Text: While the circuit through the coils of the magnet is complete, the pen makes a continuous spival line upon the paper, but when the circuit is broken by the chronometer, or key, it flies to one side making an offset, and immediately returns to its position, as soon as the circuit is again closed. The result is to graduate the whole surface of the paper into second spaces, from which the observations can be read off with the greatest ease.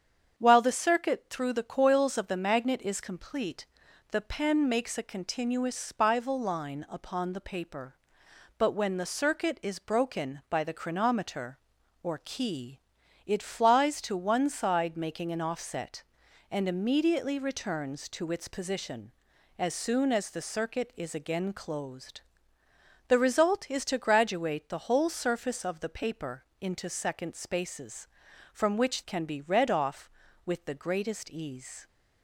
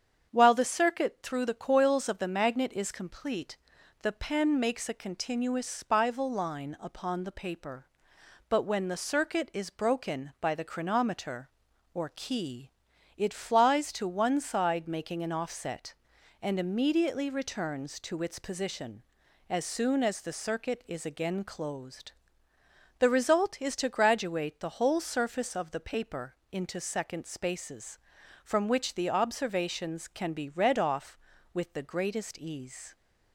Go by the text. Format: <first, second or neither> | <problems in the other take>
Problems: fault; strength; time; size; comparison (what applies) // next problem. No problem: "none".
second | starts louder than the rest; strong; until 1.4 s; 7.5 dB; strong in the second // pauses between "paper" and "into"; slight; at 26.4 s; 0.18 s long; slight in the second // skips "the observations"; at 29.0 s